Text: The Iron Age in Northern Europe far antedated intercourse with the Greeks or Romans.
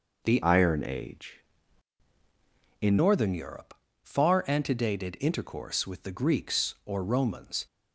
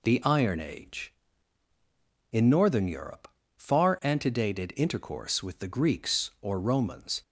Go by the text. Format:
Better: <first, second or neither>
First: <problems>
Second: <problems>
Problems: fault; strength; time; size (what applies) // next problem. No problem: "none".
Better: second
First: changes voice from "Iron" to "in"; from 0.4 to 2.9 s; 2.5 s long // pauses between "Europe" and "far"; slight; at 3.7 s; 0.28 s long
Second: pauses between "Europe" and "far"; slight; at 3.2 s; 0.28 s long